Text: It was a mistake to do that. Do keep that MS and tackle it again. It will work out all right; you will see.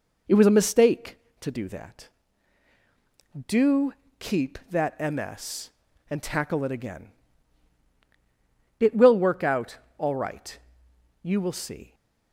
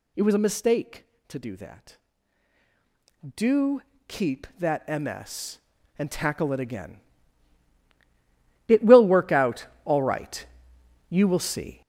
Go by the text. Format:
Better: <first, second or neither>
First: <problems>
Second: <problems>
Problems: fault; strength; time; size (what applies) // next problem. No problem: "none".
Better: first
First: pauses between "Do" and "keep"; slight; at 3.9 s; 0.26 s long // pauses between "out" and "all"; slight; at 9.7 s; 0.20 s long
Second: gets louder; strong; throughout; 7.5 dB // pauses between "Do" and "keep"; slight; at 3.8 s; 0.26 s long // pauses between "out" and "all"; slight; at 9.6 s; 0.18 s long